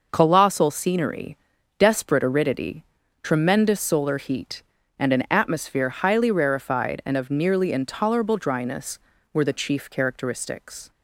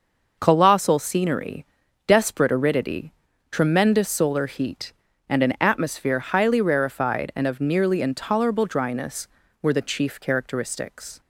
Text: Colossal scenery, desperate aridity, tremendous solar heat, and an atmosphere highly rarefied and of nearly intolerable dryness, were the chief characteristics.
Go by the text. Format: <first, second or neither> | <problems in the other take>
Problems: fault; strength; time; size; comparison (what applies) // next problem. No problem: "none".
neither | none